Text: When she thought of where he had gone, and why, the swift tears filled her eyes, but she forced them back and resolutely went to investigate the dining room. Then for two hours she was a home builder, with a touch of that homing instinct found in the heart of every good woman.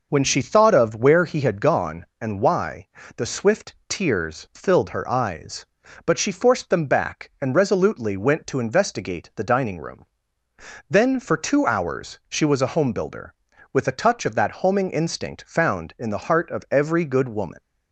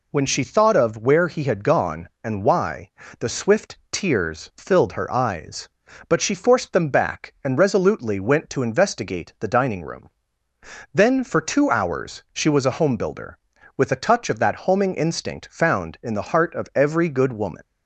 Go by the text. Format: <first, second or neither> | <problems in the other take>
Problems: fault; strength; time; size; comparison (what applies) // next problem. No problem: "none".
second | starts louder than the rest; noticeable; until 1.8 s; 6 dB